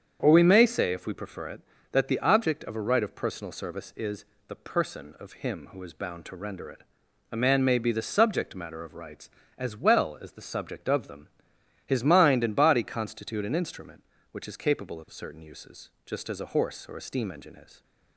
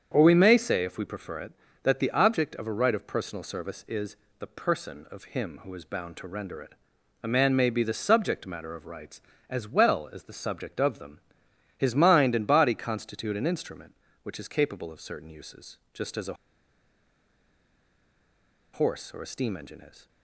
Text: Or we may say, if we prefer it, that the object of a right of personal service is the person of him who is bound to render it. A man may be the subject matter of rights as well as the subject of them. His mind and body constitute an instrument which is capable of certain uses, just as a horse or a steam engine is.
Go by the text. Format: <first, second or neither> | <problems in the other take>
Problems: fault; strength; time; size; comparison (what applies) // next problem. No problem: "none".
first | starts louder than the rest; strong; until 1.1 s; 7.5 dB; strong in the first // pauses between "is" and "the"; slight; at 4.1 s; 0.26 s long; slight in the first // pauses between "a" and "horse"; strong; at 16.3 s; 2.3 s long